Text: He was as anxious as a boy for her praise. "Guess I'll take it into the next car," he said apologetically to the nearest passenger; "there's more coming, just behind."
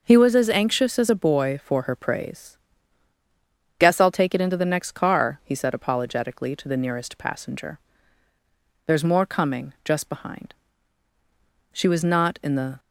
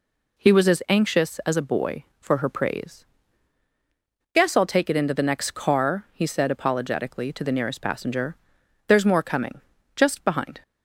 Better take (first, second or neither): second